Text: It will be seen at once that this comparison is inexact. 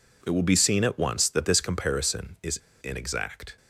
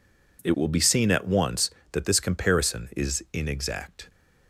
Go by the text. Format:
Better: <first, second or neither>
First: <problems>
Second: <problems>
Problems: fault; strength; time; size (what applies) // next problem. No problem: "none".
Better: second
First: pauses between "is" and "inexact"; slight; at 2.5 s; 0.23 s long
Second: none